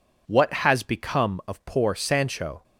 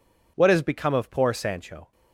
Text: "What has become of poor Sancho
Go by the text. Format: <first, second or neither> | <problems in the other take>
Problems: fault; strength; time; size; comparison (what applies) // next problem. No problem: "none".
neither | none